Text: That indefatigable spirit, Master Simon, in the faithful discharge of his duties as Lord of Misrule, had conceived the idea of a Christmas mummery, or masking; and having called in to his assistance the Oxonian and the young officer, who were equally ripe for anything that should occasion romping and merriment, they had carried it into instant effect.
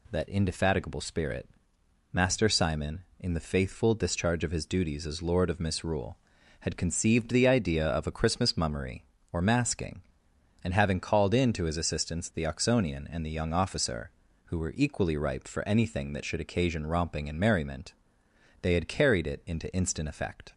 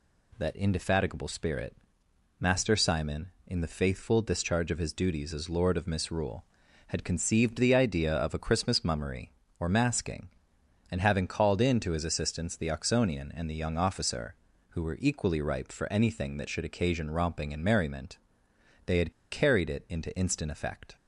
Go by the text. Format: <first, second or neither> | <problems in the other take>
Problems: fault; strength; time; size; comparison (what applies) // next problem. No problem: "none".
first | pauses between "had" and "carried"; slight; at 19.1 s; 0.18 s long